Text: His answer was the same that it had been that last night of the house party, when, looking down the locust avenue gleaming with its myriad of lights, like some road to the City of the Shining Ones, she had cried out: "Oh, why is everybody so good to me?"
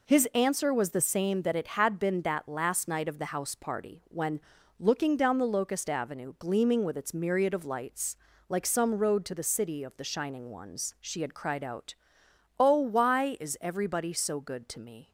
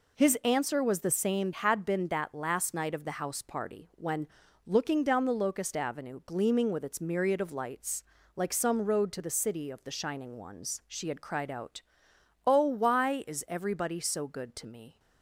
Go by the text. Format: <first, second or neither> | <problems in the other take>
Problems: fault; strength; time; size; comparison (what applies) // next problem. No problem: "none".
first | skips "that it"; at 1.5 s